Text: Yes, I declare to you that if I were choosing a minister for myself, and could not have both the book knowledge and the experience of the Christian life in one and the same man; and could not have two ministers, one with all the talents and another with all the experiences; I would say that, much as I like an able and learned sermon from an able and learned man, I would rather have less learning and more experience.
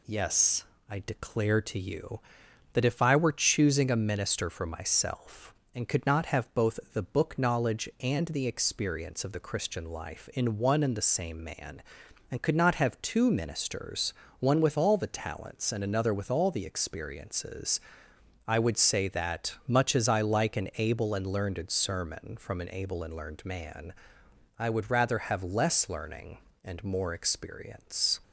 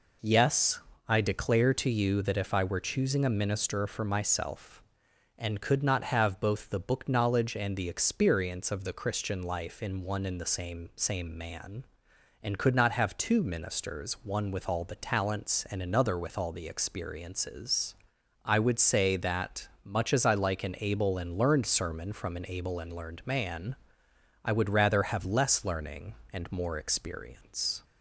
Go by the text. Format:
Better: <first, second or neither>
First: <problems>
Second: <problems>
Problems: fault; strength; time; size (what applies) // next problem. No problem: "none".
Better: first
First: none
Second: says "same" twice; at 10.9 s